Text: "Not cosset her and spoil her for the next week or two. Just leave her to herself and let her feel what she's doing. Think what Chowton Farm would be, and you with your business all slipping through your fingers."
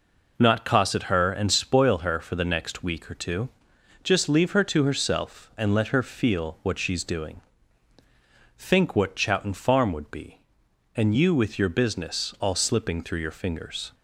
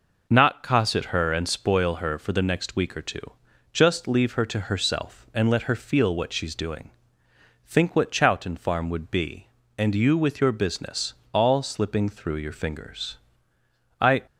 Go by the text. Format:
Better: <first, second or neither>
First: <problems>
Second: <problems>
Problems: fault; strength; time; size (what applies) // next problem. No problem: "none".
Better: first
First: none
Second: pauses between "business" and "all"; slight; at 11.1 s; 0.20 s long // goes on to say "I"; slight; from 13.9 s on; 0.22 s long